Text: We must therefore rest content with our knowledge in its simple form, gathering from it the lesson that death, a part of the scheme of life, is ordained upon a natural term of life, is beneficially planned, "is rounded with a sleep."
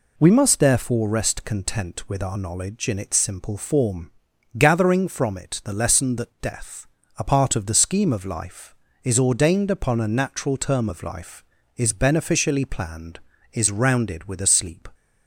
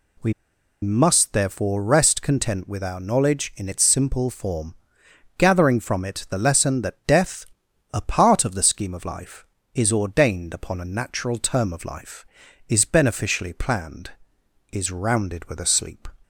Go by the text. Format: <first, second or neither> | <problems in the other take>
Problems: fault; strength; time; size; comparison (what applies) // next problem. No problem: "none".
first | pauses between "We" and "must"; noticeable; at 0.3 s; 0.49 s long